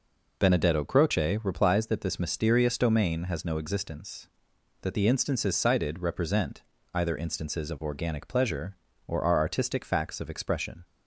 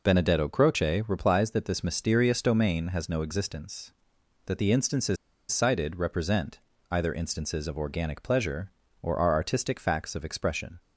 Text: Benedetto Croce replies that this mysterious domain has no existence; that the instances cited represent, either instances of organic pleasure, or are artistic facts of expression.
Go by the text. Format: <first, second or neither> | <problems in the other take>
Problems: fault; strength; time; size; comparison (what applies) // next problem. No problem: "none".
first | pauses between "instances" and "cited"; slight; at 5.1 s; 0.35 s long